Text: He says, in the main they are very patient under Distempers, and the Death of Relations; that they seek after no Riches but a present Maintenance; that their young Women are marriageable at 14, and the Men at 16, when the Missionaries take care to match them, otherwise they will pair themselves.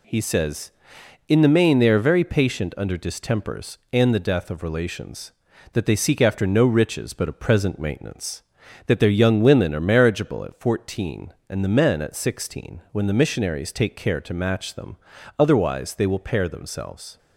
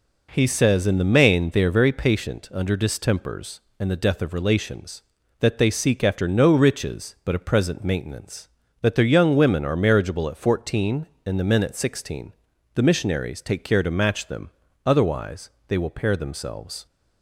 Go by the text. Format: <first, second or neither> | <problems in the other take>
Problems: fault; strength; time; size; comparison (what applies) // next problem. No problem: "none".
first | skips "when"; at 12.5 s // pauses between "otherwise" and "they"; slight; at 15.4 s; 0.18 s long